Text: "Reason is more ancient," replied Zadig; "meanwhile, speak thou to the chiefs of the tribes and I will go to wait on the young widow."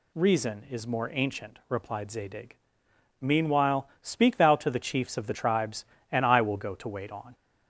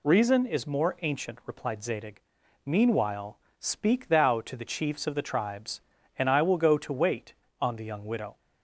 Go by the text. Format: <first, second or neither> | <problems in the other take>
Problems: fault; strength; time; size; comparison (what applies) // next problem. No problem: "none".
second | stops before "the young widow"; at 7.3 s